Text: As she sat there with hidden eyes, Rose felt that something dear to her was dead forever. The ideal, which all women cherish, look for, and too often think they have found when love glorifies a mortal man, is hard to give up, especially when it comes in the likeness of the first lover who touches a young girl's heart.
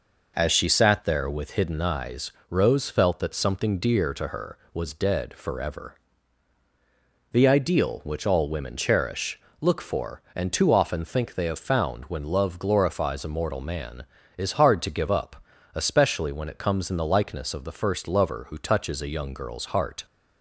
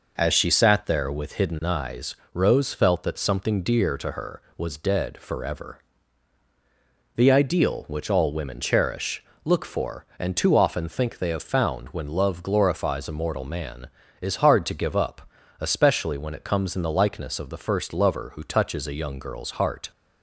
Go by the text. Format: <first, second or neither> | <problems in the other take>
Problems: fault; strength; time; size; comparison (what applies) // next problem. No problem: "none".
neither | none